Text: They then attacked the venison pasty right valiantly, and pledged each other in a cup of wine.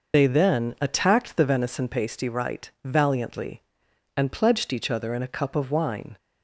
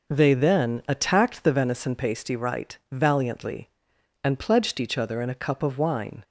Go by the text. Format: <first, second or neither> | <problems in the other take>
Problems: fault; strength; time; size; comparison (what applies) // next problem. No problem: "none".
second | loses the start of "They"; at 0.1 s; 125 ms // pauses between "right" and "valiantly"; slight; at 2.6 s; 0.16 s long; slight in the second